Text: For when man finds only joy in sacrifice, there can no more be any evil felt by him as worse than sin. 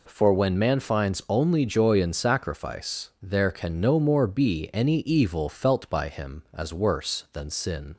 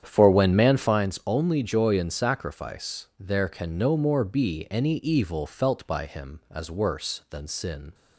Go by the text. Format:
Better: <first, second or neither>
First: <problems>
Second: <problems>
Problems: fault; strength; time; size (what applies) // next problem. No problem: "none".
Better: first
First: none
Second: starts louder than the rest; strong; until 1.1 s; 9 dB